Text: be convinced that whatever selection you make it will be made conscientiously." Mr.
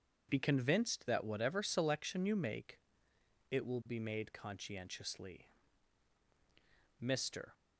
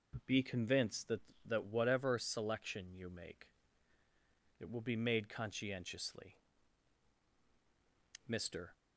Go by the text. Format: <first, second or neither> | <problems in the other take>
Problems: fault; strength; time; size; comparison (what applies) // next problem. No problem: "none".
first | says "that" twice; at 1.4 s // pauses between "make" and "it"; at 3.4 s; 1.1 s long; noticeable in the first